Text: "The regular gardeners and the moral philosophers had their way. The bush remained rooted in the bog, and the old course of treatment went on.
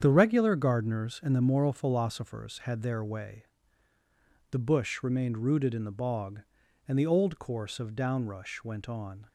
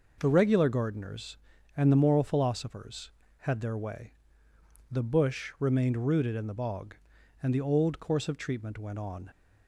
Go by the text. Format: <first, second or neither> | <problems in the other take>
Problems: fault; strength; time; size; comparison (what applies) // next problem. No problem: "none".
second | starts louder than the rest; strong; until 1.0 s; 8 dB // says "downrush" for "treatment"; at 7.9 s